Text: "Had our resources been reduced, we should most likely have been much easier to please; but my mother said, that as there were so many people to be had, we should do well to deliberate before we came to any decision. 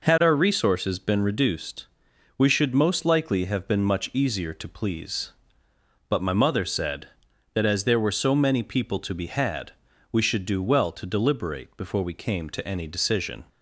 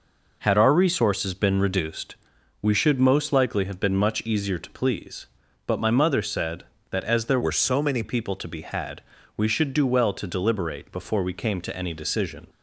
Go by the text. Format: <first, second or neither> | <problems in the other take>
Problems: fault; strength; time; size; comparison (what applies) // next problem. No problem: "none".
first | changes voice from "were" to "many"; from 7.4 to 8.0 s; 0.6 s long